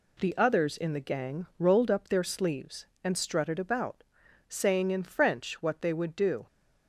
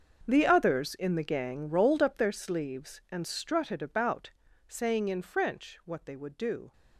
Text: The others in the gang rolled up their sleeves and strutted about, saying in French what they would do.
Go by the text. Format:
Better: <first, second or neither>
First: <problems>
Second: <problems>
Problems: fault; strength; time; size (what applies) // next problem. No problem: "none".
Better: first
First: none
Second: gets quieter; strong; throughout; 16.5 dB